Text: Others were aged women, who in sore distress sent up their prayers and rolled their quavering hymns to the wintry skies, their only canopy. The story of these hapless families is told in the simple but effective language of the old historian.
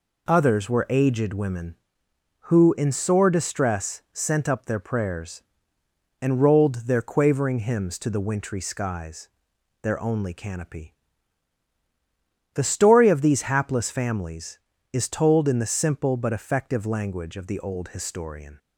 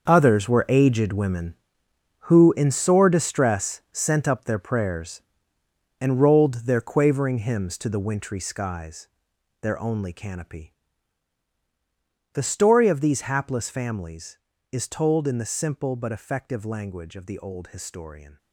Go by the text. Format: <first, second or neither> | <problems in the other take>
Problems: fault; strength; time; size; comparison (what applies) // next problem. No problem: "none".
first | gets quieter; strong; throughout; 13 dB